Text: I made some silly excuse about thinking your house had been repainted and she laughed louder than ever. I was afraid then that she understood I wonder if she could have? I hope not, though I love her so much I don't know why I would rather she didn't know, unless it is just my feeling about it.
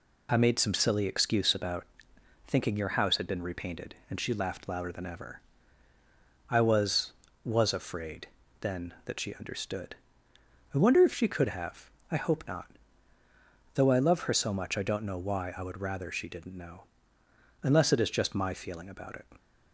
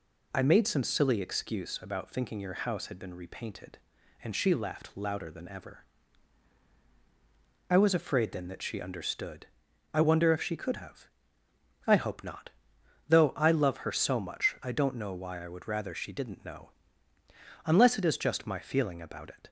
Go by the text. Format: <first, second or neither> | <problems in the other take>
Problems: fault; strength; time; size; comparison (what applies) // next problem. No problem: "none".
second | pauses between "about" and "thinking"; noticeable; at 1.8 s; 0.62 s long // says "was" twice; at 7.4 s // pauses between "afraid" and "then"; slight; at 8.2 s; 0.32 s long // pauses between "understood" and "I"; noticeable; at 9.9 s; 0.80 s long; also in the second